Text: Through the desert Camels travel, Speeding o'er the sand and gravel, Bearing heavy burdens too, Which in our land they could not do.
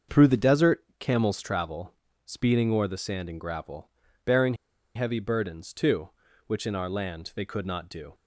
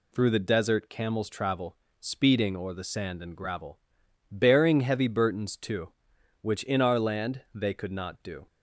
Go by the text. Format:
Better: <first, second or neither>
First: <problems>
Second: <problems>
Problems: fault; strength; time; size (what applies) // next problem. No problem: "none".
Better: second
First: starts louder than the rest; until 1.2 s; 6.5 dB // pauses between "Bearing" and "heavy"; at 4.5 s; 0.41 s long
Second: none